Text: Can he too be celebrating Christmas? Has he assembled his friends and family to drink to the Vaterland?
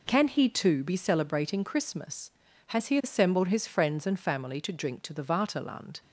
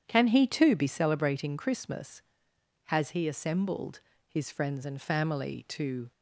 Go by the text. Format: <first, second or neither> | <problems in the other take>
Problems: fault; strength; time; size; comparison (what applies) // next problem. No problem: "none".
first | starts louder than the rest; strong; until 1.0 s; 9 dB // pauses between "assembled" and "his"; slight; at 3.9 s; 0.28 s long // stops before "drink to the Vaterland"; at 6.1 s